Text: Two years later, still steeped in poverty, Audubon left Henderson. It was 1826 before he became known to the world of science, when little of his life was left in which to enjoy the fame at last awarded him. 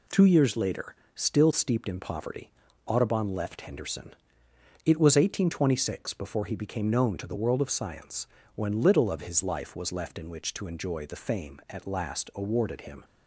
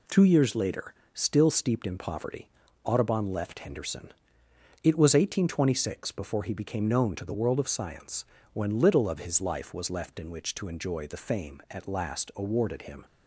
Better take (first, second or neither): neither